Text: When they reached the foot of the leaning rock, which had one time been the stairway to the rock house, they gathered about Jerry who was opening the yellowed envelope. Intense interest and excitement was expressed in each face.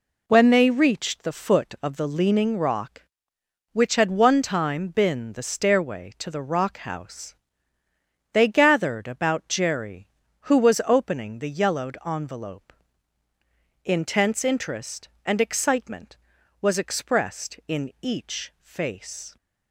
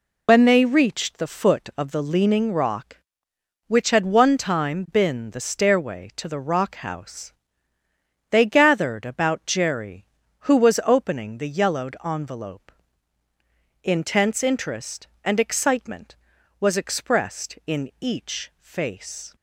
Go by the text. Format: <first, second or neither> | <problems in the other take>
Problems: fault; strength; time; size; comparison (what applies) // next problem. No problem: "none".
first | loses the start of "When"; at 0.2 s; 60 ms